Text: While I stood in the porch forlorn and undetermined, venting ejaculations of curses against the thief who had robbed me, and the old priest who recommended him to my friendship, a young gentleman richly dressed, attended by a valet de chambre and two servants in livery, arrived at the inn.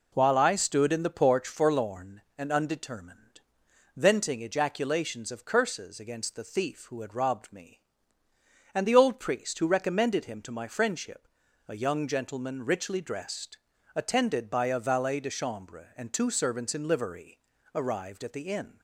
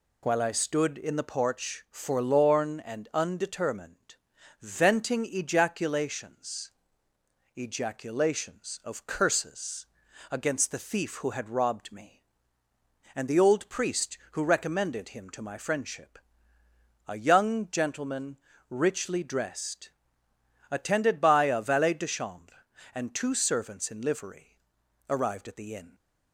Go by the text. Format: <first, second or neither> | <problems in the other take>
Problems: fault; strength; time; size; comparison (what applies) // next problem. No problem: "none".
first | says "ejaculations" twice; at 7.5 s // pauses between "curses" and "against"; noticeable; at 9.8 s; 0.46 s long // pauses between "gentleman" and "richly"; slight; at 18.3 s; 0.32 s long